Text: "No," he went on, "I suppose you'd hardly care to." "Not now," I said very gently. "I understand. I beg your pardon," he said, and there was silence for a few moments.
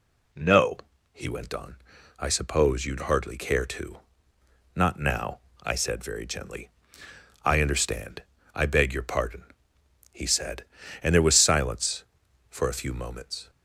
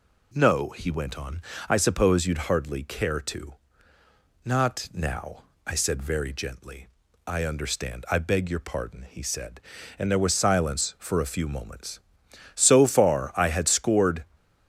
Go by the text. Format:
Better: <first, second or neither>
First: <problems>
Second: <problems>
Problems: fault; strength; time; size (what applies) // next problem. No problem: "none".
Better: first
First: none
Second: goes on to say "So far I had scored"; strong; from 12.5 s on; 1.7 s long